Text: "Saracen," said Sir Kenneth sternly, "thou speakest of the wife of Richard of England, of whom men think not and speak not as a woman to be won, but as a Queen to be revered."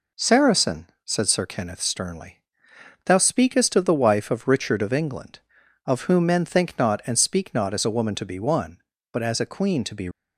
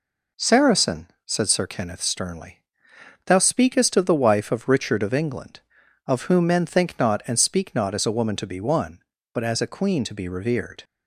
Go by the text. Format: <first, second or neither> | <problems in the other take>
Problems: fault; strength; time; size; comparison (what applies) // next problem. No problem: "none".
second | stops before "revered"; at 10.1 s